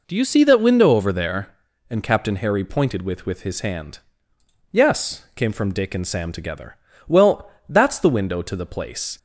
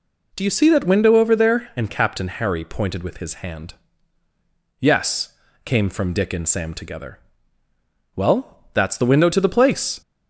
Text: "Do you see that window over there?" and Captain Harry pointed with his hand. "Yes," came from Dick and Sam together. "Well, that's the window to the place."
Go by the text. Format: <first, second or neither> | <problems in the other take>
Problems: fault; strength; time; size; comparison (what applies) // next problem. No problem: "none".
second | says "with" twice; at 3.2 s